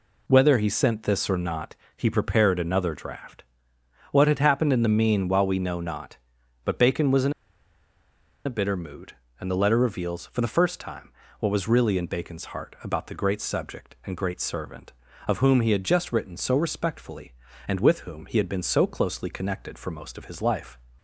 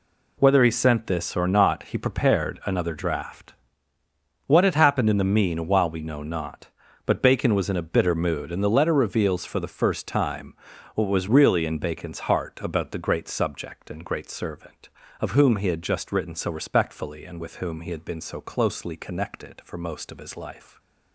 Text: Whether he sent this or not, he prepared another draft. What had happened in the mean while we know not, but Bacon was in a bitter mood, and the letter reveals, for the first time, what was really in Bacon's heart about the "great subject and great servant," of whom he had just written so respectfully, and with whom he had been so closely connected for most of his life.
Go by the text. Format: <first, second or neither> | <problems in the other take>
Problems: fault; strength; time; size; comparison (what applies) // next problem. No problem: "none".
second | pauses between "in" and "a"; at 7.3 s; 1.1 s long